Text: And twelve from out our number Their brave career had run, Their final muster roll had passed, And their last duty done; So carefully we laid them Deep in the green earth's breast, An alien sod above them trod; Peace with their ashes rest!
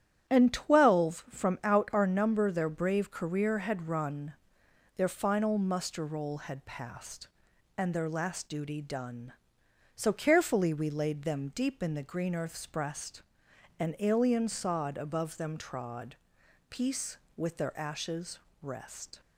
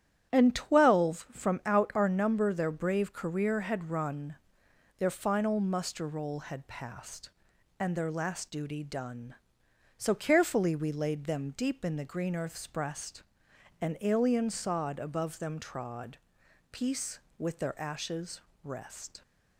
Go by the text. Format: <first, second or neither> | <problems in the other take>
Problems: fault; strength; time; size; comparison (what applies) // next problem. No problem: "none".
neither | starts louder than the rest; strong; the same in both // pauses between "ashes" and "rest"; slight; the same in both